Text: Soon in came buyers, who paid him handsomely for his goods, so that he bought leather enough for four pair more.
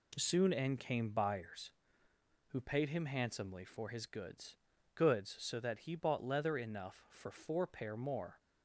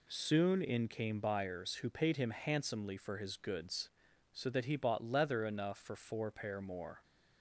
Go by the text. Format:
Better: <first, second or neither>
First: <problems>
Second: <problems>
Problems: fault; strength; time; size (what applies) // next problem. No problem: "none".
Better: second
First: says "goods" twice; at 4.9 s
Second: none